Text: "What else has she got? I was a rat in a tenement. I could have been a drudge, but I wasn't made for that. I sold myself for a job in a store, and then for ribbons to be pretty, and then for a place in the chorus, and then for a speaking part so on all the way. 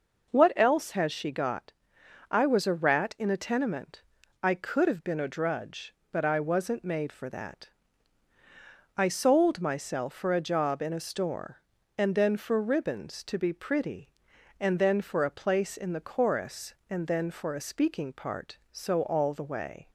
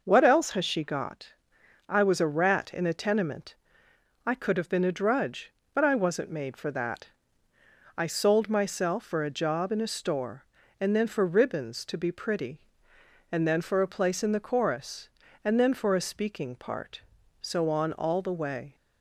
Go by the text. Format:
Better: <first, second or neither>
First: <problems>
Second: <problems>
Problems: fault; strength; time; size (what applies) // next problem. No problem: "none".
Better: second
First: skips "on"; at 19.0 s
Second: none